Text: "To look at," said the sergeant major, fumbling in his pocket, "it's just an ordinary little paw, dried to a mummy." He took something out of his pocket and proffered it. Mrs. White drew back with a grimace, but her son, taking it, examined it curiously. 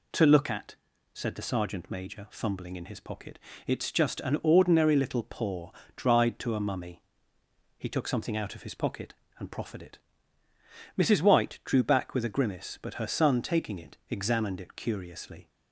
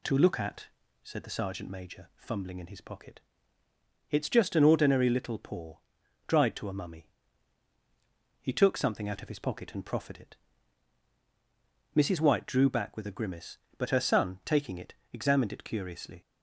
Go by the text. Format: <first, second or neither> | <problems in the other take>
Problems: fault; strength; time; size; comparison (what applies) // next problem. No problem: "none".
neither | none